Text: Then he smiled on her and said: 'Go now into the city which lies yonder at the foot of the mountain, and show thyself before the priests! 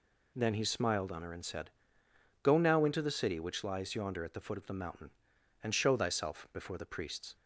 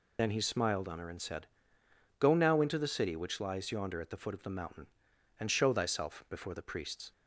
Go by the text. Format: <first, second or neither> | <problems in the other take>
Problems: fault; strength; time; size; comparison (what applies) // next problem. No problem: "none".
first | loses the start of "Then"; at 0.1 s; 75 ms